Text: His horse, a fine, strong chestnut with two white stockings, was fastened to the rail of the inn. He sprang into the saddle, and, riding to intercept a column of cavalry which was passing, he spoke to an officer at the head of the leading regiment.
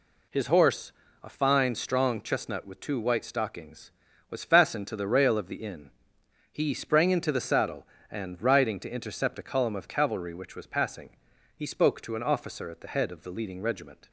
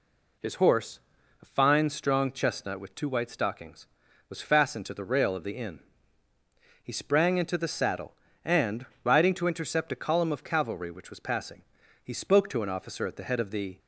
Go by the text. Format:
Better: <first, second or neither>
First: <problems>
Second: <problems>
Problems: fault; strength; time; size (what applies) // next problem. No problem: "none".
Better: first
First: none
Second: stops before "leading regiment"; at 13.7 s